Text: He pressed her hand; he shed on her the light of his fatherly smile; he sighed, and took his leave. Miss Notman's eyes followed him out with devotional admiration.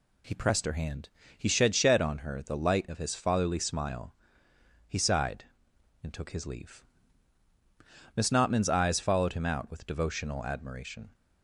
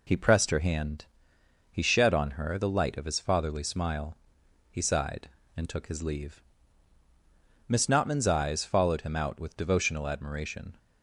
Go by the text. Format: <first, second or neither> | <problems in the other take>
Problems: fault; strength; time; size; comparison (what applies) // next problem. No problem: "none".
second | says "shed" twice; at 1.7 s